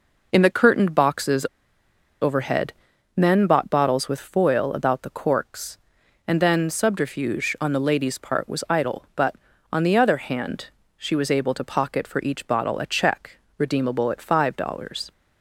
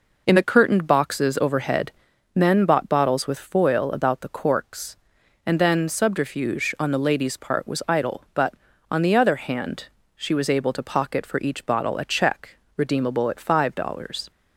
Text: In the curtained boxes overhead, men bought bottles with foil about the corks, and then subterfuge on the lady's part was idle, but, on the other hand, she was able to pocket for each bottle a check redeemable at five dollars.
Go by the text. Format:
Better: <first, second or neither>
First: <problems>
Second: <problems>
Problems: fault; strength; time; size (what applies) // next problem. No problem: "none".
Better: second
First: pauses between "boxes" and "overhead"; noticeable; at 1.4 s; 0.75 s long // pauses between "check" and "redeemable"; slight; at 13.3 s; 0.20 s long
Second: pauses between "check" and "redeemable"; slight; at 12.5 s; 0.20 s long